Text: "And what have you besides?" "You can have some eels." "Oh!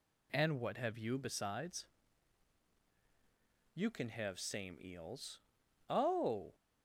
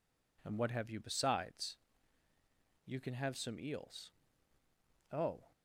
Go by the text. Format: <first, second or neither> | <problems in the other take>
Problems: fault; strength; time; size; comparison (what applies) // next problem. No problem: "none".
second | says "same" for "some"; at 4.3 s